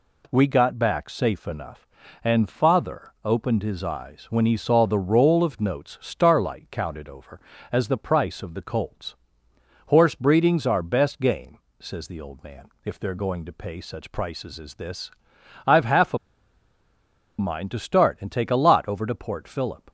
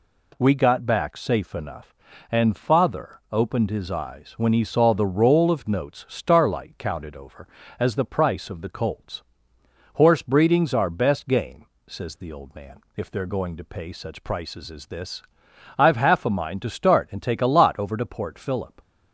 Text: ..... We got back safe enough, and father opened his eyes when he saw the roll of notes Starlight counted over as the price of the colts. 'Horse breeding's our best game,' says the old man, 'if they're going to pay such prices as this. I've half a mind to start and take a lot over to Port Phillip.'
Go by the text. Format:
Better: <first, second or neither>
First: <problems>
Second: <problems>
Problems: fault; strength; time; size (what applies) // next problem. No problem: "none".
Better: second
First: pauses between "a" and "mind"; at 16.1 s; 1.2 s long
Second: none